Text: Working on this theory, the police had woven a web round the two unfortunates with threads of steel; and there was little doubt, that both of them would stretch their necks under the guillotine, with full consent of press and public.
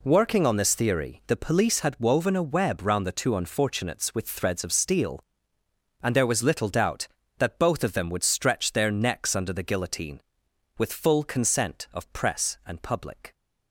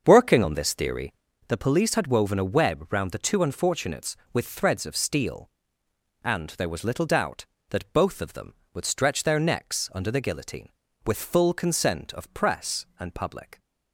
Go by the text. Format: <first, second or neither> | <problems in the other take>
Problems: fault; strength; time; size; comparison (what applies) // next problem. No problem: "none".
first | starts louder than the rest; until 1.4 s; 6.5 dB